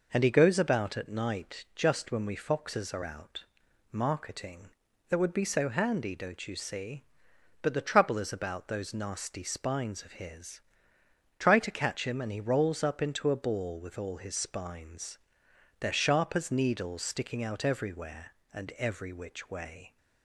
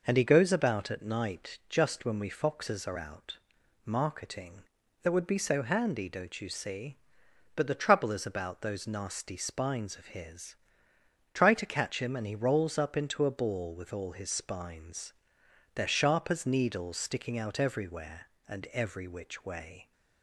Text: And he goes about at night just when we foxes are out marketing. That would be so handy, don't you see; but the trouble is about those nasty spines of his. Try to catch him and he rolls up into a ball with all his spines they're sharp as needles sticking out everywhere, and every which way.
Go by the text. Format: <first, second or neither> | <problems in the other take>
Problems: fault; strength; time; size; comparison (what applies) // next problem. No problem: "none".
neither | pauses between "out" and "marketing"; noticeable; the same in both // pauses between "spines" and "they're"; noticeable; the same in both